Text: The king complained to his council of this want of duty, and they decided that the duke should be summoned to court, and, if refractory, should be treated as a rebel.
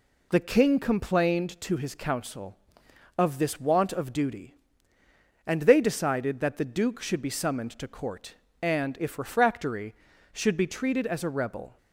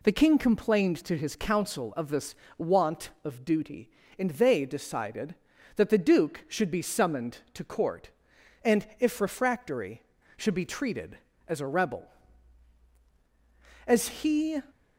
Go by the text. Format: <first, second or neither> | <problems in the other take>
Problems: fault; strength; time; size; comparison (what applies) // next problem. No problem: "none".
first | pauses between "this" and "want"; slight; at 2.3 s; 0.24 s long // goes on to say "As he"; noticeable; from 13.8 s on; 0.76 s long